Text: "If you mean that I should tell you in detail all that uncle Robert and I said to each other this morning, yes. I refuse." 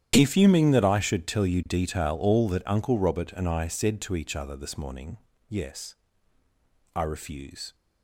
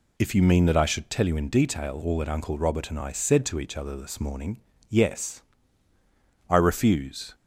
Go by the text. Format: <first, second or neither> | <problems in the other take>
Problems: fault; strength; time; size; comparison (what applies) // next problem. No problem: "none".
second | starts louder than the rest; strong; until 1.1 s; 10.5 dB // skips "in"; at 1.6 s